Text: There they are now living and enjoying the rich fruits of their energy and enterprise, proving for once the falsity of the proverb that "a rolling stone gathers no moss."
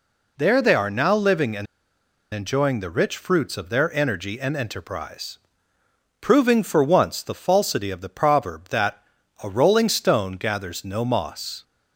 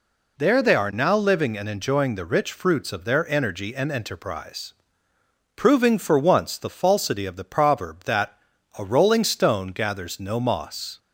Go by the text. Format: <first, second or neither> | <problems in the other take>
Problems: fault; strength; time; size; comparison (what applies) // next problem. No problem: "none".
second | pauses between "and" and "enjoying"; noticeable; at 1.6 s; 0.67 s long // pauses between "that" and "a"; at 9.0 s; 0.40 s long; also in the second